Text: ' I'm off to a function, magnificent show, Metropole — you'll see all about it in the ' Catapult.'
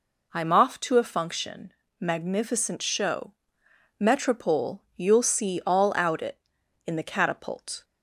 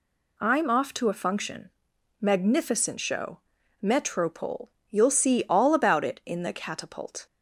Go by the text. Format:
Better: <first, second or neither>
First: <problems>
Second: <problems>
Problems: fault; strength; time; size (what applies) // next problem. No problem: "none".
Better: second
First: says "out" for "about"; at 5.9 s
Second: none